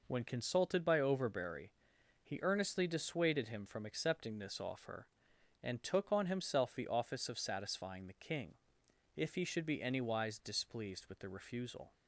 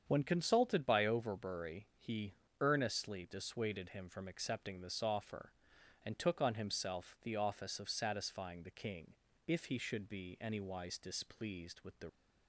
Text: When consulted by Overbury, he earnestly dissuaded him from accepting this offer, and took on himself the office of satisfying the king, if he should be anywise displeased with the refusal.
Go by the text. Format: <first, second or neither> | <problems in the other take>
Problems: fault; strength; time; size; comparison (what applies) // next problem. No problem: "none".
first | starts louder than the rest; strong; until 1.0 s; 7.5 dB // pauses between "he" and "earnestly"; slight; at 2.3 s; 0.26 s long // stops before "refusal"; at 12.0 s